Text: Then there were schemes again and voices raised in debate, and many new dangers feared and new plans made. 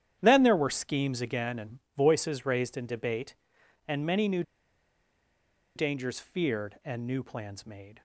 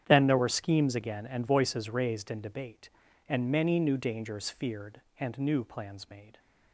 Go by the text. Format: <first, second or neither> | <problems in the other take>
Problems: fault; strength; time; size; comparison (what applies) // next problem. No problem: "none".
second | starts louder than the rest; strong; until 1.2 s; 10 dB; strong in the second // pauses between "and" and "voices"; slight; at 1.7 s; 0.18 s long // pauses between "new" and "dangers"; strong; at 4.4 s; 1.3 s long